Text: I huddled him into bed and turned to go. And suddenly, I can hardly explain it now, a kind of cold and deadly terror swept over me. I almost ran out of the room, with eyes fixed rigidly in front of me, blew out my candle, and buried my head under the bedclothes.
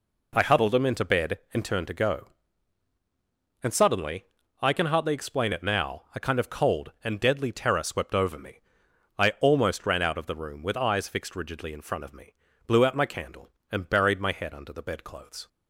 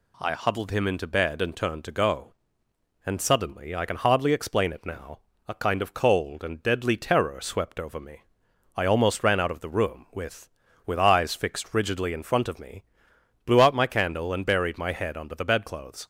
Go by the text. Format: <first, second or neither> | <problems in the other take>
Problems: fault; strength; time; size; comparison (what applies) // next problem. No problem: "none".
first | says "with" twice; at 10.8 s